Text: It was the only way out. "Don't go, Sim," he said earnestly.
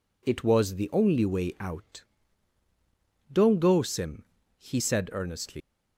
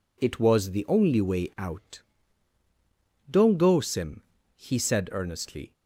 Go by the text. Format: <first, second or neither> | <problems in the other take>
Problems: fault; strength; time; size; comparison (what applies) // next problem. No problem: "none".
second | leaves "earnestly" unfinished; at 5.6 s; 125 ms